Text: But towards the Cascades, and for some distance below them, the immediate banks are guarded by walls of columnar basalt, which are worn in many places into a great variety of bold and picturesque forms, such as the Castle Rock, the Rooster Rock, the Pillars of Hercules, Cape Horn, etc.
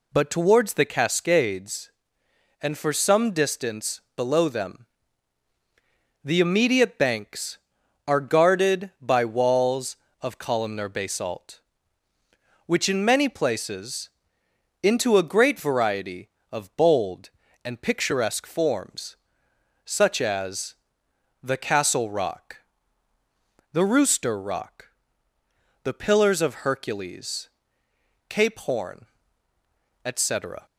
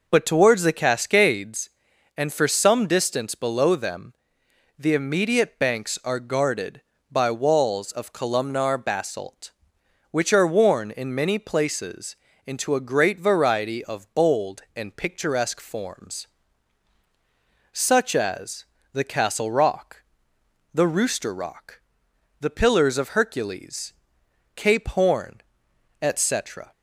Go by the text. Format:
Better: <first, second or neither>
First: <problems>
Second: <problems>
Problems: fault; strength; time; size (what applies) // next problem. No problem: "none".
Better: second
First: pauses between "distance" and "below"; slight; at 4.0 s; 0.16 s long // skips "are worn"; at 12.8 s // pauses between "places" and "into"; noticeable; at 14.0 s; 0.74 s long // pauses between "as" and "the"; noticeable; at 20.7 s; 0.66 s long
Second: pauses between "places" and "into"; slight; at 12.1 s; 0.30 s long // pauses between "as" and "the"; slight; at 18.6 s; 0.26 s long